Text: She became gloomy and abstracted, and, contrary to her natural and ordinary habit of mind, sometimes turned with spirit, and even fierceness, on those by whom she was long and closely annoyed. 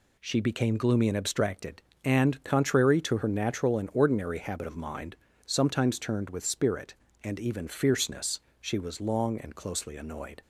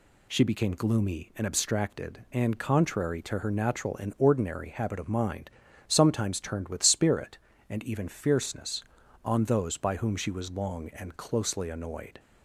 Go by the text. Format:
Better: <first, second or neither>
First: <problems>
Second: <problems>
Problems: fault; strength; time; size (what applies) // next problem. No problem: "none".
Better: second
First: skips "on those by whom"; at 8.4 s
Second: none